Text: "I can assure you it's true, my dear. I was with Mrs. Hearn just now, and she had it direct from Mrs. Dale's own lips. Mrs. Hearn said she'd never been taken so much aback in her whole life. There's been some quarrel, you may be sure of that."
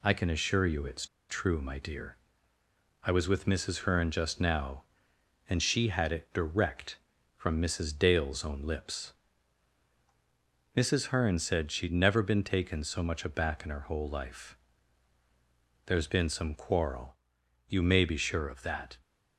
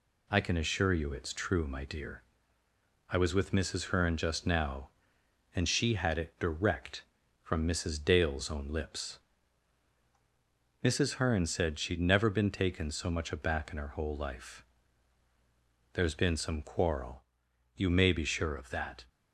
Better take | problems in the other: second | pauses between "it's" and "true"; slight; at 1.0 s; 0.24 s long

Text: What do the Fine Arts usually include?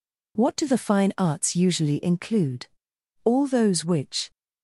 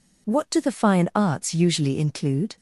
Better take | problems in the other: second | goes on to say "All those which"; noticeable; from 3.2 s on; 1.0 s long

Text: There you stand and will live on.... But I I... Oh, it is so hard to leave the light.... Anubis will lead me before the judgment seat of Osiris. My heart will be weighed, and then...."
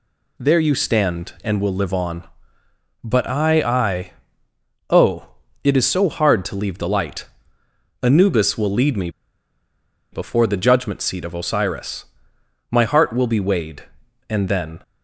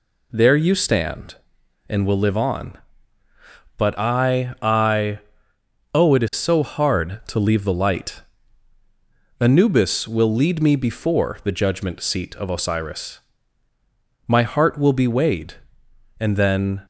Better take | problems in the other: second | pauses between "me" and "before"; at 9.0 s; 1.0 s long

